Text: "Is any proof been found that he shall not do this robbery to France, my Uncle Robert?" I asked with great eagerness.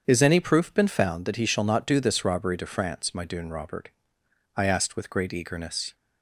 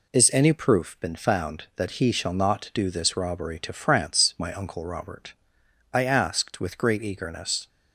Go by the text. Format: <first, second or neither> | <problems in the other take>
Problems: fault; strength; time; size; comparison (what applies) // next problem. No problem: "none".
second | starts louder than the rest; strong; until 1.0 s; 7.5 dB // says "Dune" for "Uncle"; at 3.2 s